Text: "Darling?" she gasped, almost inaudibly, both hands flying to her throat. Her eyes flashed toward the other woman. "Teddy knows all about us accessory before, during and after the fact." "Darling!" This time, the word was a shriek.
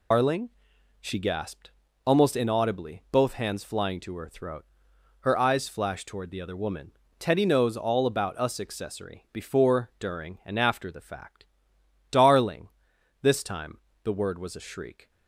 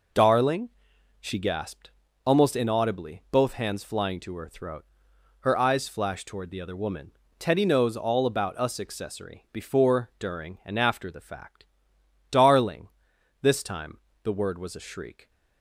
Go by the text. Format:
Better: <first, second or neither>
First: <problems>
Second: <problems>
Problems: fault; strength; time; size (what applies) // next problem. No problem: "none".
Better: second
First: loses the start of "Darling"; at 0.1 s; 165 ms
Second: none